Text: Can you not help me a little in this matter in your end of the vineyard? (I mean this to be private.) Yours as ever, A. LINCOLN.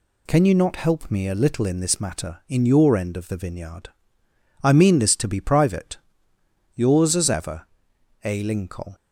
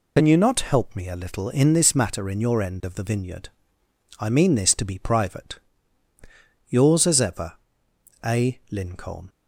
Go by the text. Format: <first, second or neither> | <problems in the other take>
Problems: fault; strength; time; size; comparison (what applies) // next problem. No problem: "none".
first | loses the start of "Can"; at 0.1 s; 80 ms